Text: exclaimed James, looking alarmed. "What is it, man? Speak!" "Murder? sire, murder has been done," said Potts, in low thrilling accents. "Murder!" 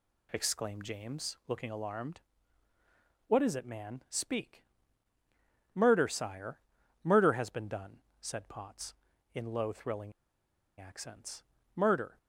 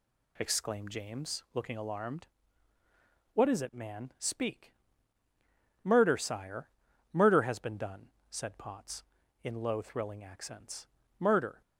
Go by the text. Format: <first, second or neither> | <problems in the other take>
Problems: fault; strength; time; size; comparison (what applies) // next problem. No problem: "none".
second | pauses between "thrilling" and "accents"; noticeable; at 10.1 s; 0.67 s long